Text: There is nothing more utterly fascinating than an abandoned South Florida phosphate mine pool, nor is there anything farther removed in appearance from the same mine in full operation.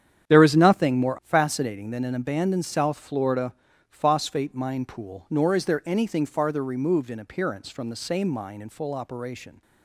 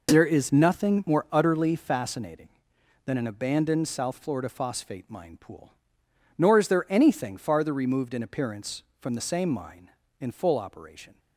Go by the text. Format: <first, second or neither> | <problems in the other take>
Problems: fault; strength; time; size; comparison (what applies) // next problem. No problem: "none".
second | starts louder than the rest; strong; until 1.3 s; 9 dB // skips "utterly"; at 1.2 s // pauses between "Florida" and "phosphate"; slight; at 3.5 s; 0.36 s long